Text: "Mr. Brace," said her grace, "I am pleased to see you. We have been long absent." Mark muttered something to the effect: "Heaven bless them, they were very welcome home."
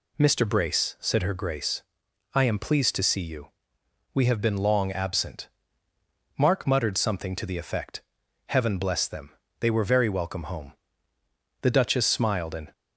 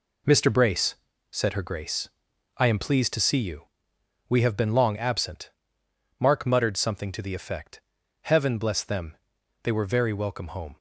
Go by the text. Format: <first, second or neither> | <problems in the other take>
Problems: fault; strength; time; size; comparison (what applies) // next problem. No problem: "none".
second | goes on to say "The duchess smiled and"; noticeable; from 11.6 s on; 1.1 s long